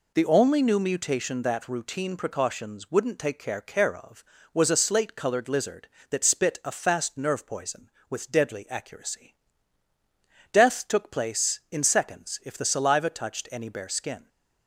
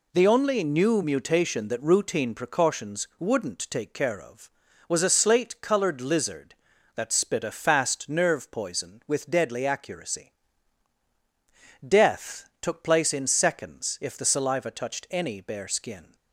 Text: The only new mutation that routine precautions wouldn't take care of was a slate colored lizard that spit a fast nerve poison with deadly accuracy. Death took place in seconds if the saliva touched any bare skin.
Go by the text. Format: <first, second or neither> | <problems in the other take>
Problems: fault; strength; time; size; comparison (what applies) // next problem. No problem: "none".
second | says "care" twice; at 3.6 s